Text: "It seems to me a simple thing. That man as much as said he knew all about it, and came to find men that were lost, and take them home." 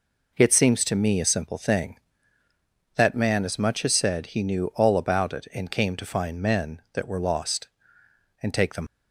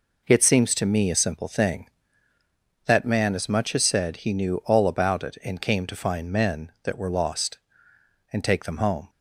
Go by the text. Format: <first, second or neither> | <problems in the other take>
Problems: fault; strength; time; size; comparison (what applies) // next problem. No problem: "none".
second | stops before "home"; at 8.8 s